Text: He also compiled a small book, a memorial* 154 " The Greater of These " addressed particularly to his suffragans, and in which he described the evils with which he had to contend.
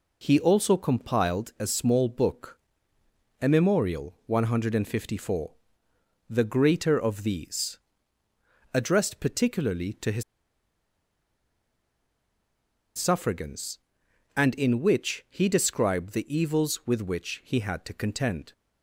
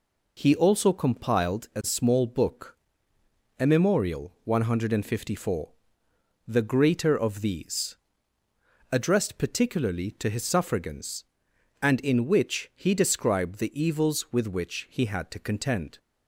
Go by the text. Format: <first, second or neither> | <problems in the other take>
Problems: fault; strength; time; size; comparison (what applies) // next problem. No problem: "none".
second | pauses between "his" and "suffragans"; strong; at 10.2 s; 2.7 s long